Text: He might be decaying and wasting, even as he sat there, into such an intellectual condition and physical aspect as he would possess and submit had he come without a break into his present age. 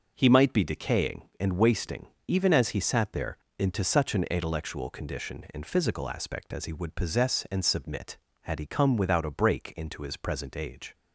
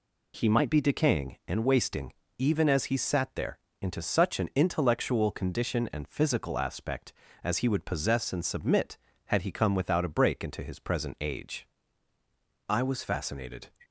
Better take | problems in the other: first | goes on to say "I was fascinated"; noticeable; from 12.6 s on; 1.0 s long

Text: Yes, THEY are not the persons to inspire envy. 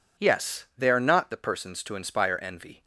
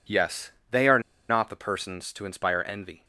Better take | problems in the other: first | pauses between "are" and "not"; slight; at 0.9 s; 0.29 s long

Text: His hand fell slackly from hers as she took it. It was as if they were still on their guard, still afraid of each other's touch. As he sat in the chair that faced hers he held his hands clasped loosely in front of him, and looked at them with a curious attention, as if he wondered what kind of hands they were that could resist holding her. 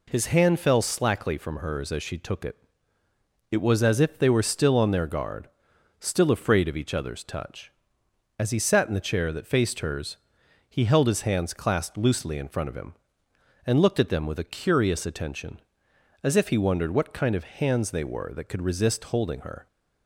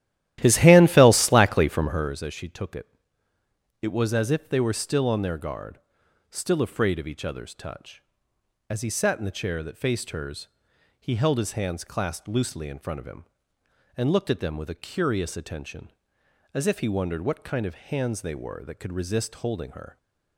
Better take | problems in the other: first | starts louder than the rest; strong; until 2.2 s; 13.5 dB // pauses between "hers" and "he"; noticeable; at 10.4 s; 0.54 s long; noticeable in the first

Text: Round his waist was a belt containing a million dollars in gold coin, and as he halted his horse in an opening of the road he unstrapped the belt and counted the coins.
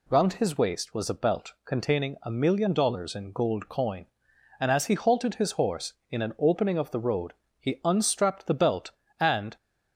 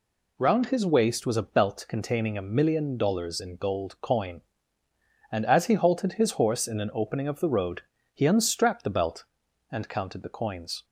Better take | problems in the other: second | pauses between "road" and "he"; slight; at 7.3 s; 0.24 s long; slight in the second // stops before "counted the coins"; at 9.5 s

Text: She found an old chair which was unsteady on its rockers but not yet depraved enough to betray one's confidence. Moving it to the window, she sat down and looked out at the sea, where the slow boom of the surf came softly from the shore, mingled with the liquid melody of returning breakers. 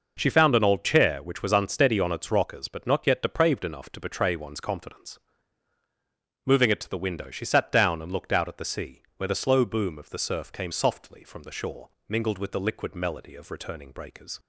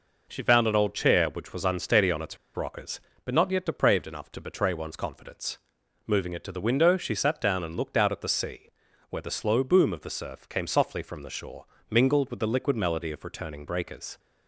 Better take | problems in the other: first | pauses between "its" and "rockers"; slight; at 2.3 s; 0.19 s long

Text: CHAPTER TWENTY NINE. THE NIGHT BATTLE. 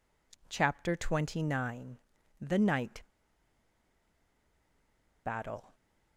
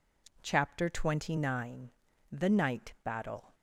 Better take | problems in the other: second | pauses between "NIGHT" and "BATTLE"; strong; at 3.0 s; 2.2 s long

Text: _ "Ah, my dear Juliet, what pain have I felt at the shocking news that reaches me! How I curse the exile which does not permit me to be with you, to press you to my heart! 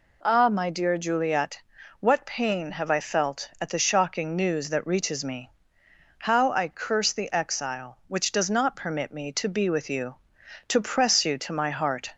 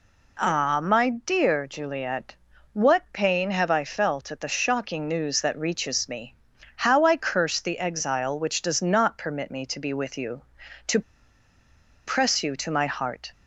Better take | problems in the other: first | pauses between "to" and "press"; at 10.9 s; 1.0 s long

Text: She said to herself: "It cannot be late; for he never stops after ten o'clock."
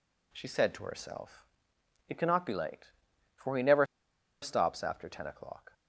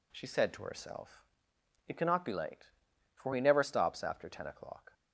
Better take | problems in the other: second | pauses between "never" and "stops"; noticeable; at 3.8 s; 0.57 s long

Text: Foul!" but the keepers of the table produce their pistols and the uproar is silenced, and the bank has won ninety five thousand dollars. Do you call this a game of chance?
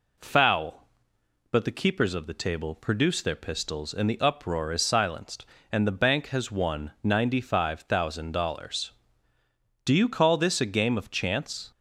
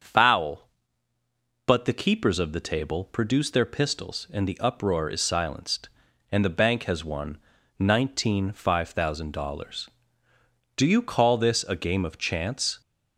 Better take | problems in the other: first | starts louder than the rest; until 1.9 s; 6.5 dB // says "nineteen" for "ninety"; at 7.7 s

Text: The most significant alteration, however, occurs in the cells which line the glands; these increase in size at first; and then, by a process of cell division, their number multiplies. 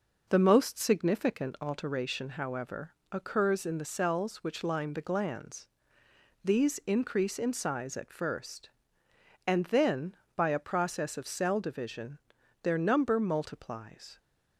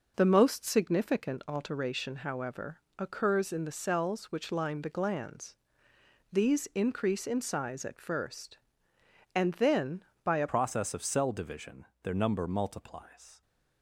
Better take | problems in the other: first | changes voice at "process"; from 10.5 s on; 2.9 s long

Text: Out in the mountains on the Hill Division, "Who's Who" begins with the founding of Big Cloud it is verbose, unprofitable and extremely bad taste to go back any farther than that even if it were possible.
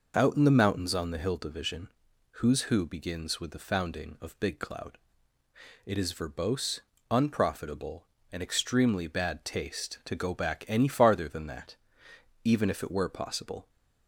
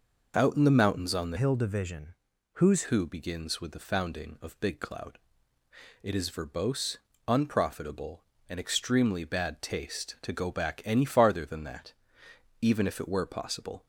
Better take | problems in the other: first | changes voice from "Hill" to "Who's"; from 1.3 to 2.8 s; 1.5 s long // pauses between "Cloud" and "it"; noticeable; at 5.1 s; 0.84 s long; noticeable in the first // pauses between "that" and "even"; noticeable; at 11.9 s; 0.66 s long; noticeable in the first

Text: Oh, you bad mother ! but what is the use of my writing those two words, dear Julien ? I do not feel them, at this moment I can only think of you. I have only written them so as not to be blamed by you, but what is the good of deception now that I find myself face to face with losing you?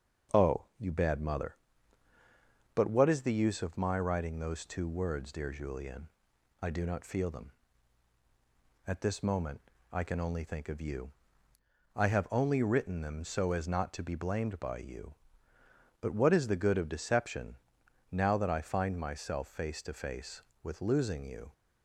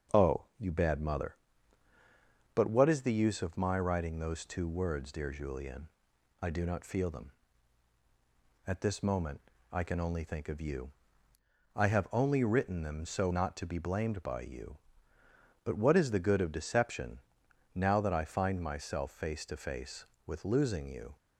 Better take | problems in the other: first | starts louder than the rest; until 1.2 s; 6 dB; also in the first // pauses between "moment" and "I"; slight; at 9.3 s; 0.32 s long; slight in the first // skips "as"; at 13.3 s // pauses between "deception" and "now"; noticeable; at 17.1 s; 0.54 s long; noticeable in the first

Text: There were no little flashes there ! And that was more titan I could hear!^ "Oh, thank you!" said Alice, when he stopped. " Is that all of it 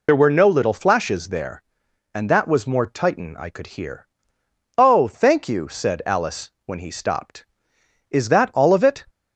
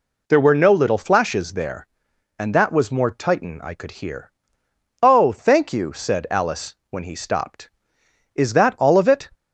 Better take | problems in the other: second | loses the start of "There"; at 0.0 s; 55 ms

